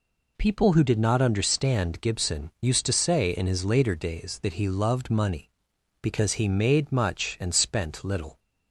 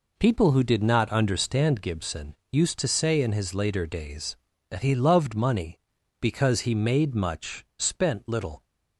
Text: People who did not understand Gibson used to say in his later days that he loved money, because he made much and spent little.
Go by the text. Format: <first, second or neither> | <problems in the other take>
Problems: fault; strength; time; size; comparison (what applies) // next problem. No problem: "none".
first | skips "and"; at 7.7 s